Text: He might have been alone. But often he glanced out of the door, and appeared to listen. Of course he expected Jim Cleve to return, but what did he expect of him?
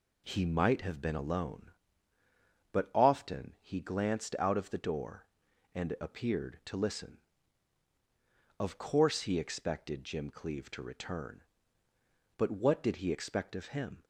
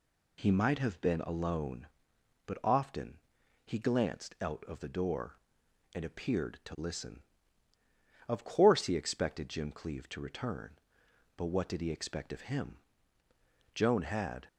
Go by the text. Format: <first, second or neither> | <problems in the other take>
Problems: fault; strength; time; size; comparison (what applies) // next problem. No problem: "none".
first | pauses between "often" and "he"; noticeable; at 3.1 s; 0.48 s long // goes on to say "Joan had"; noticeable; from 13.7 s on; 0.72 s long